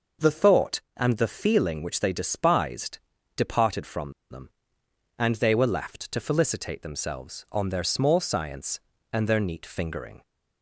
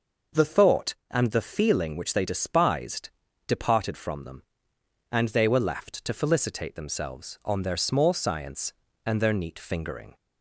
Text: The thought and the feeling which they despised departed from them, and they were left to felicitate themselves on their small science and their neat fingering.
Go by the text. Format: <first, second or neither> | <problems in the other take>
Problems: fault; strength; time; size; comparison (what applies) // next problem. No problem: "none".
second | pauses between "despised" and "departed"; at 2.9 s; 0.40 s long; also in the second // pauses between "from" and "them"; slight; at 4.1 s; 0.18 s long